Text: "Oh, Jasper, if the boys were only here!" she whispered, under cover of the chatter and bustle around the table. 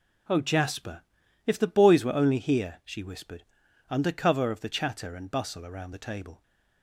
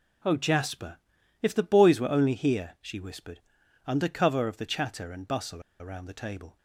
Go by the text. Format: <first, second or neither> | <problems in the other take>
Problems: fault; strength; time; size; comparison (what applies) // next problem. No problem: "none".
first | pauses between "bustle" and "around"; slight; at 5.6 s; 0.19 s long